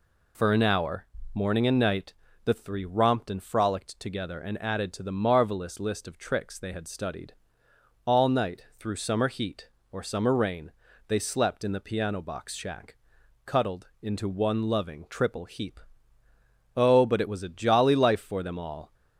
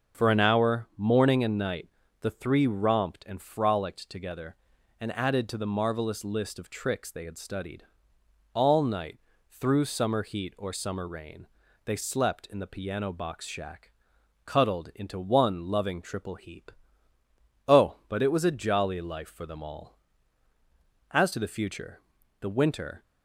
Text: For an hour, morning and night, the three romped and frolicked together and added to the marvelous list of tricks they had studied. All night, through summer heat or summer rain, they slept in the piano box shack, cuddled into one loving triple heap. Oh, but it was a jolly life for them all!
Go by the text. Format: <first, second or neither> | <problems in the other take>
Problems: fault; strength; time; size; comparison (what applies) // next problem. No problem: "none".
first | starts louder than the rest; until 1.2 s; 6.5 dB // goes on to say "As to the future the winter"; strong; from 21.1 s on; 1.9 s long